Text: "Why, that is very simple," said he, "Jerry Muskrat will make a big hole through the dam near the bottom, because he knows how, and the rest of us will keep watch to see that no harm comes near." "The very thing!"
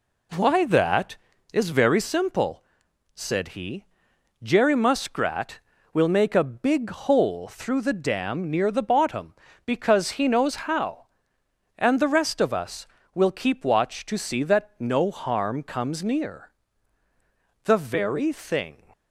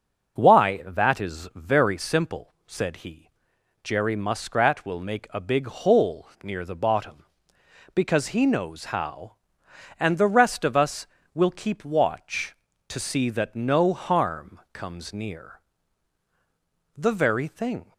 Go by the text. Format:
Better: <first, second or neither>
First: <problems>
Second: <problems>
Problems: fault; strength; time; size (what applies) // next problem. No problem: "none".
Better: first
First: none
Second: skips "through the dam"; at 6.3 s